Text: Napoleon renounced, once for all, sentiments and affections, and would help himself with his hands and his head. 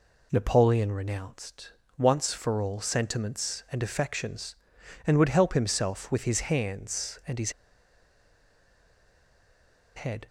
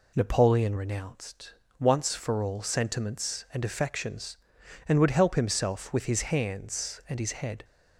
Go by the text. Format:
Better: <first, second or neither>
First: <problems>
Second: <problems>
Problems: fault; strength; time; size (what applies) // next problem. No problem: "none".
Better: second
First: pauses between "his" and "head"; strong; at 7.5 s; 2.4 s long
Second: none